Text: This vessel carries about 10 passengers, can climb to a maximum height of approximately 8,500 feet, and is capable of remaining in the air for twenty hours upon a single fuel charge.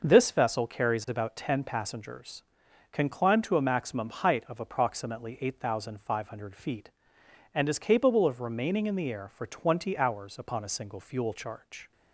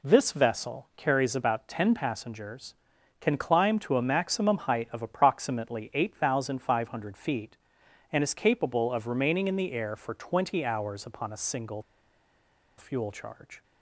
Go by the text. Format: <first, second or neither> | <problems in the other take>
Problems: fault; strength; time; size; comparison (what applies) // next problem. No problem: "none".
first | pauses between "single" and "fuel"; noticeable; at 11.8 s; 0.96 s long